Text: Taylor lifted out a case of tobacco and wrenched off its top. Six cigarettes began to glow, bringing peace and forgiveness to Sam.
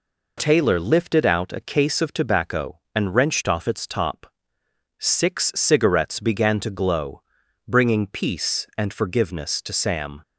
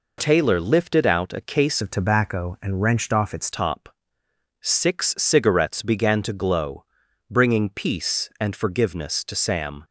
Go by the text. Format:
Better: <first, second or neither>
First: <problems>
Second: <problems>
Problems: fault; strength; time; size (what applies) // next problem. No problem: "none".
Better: first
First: none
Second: changes voice from "of" to "its"; from 1.8 to 3.4 s; 1.6 s long